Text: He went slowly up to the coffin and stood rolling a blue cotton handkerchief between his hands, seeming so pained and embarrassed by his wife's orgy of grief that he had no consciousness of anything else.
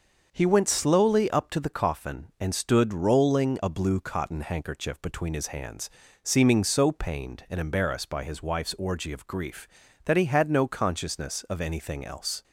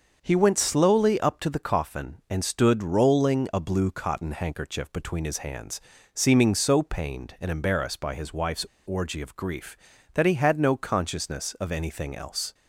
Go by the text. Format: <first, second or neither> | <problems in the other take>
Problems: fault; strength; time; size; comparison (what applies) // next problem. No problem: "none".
first | starts louder than the rest; until 1.2 s; 6 dB; also in the first // pauses between "wife's" and "orgy"; slight; at 8.6 s; 0.20 s long